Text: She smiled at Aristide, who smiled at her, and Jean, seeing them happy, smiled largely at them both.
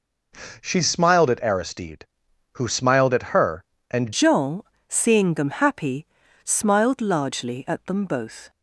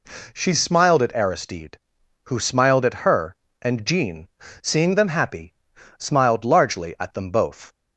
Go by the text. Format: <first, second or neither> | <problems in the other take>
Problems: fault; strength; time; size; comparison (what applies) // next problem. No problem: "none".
second | changes voice at "Jean"; from 4.1 s on; 4.3 s long